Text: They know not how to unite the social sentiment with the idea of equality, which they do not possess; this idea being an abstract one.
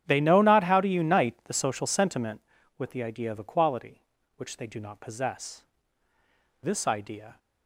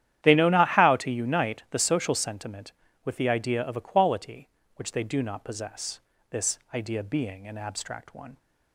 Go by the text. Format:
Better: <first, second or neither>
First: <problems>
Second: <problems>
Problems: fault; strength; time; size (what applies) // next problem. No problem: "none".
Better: second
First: starts louder than the rest; strong; until 1.0 s; 9.5 dB // stops before "being an abstract one"; at 7.3 s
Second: starts louder than the rest; strong; until 1.2 s; 11 dB